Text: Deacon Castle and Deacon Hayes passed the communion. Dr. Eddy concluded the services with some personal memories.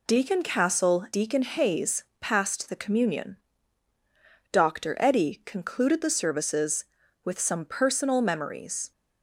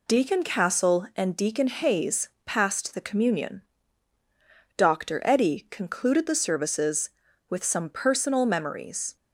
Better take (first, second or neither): second